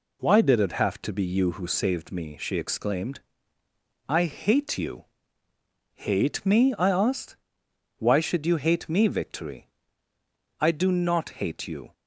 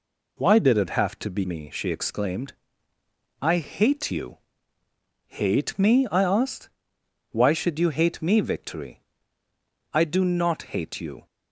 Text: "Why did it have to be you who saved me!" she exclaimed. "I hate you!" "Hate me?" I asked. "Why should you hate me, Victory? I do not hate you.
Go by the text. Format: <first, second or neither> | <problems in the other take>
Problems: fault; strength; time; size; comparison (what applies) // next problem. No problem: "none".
first | skips "you who saved"; at 1.4 s